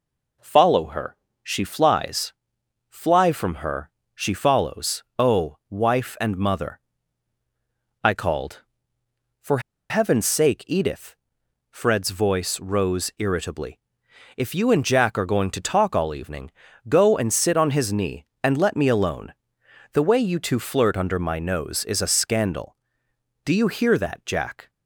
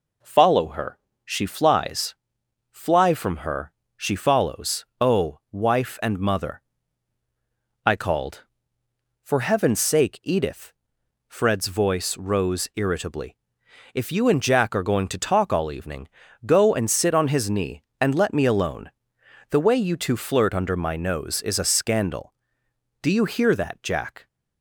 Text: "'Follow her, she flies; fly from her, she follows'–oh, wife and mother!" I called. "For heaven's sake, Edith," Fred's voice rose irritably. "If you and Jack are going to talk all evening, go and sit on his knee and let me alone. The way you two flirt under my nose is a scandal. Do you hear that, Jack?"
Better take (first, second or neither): second